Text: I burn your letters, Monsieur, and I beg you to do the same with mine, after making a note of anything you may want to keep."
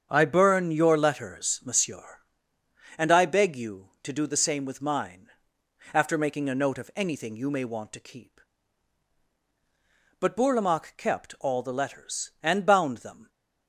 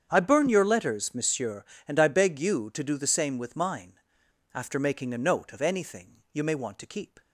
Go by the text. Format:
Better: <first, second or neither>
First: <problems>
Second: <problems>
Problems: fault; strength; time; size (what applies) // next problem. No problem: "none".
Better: second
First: starts louder than the rest; strong; until 1.1 s; 7.5 dB // goes on to say "But Bourlamaque kept all the letters and bound them"; strong; from 10.1 s on; 3.1 s long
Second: starts louder than the rest; strong; until 1.1 s; 8 dB